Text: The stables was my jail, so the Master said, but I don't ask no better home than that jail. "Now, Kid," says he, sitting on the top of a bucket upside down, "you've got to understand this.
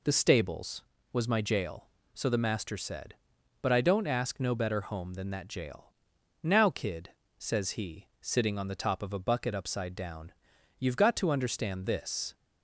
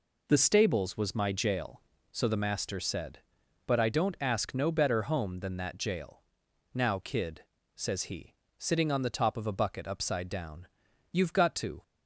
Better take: first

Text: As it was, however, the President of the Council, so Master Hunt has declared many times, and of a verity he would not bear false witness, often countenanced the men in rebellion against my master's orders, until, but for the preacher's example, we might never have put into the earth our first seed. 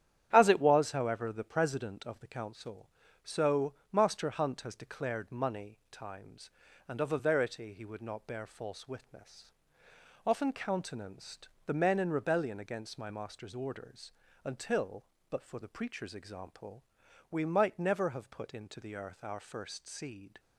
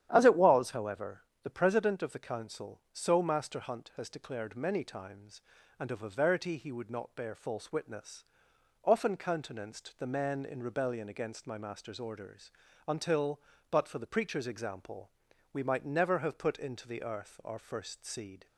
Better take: second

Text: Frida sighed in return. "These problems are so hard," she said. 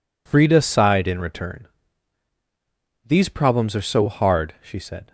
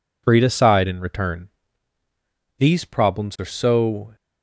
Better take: first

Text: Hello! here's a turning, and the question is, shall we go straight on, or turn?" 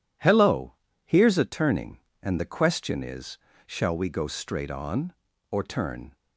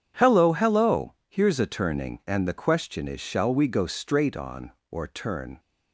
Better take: first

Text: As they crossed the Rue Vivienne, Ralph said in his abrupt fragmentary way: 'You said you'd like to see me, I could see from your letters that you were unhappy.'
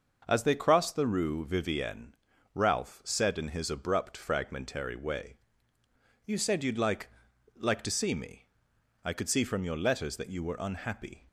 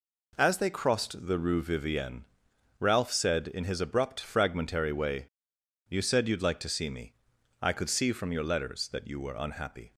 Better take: second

